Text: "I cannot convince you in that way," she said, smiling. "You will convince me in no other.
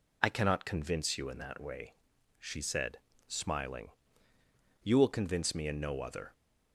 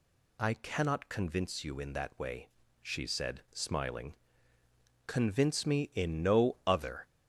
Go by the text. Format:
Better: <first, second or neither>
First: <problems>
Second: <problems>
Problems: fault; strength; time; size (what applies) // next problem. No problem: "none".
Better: first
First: none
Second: skips "You will"; at 4.6 s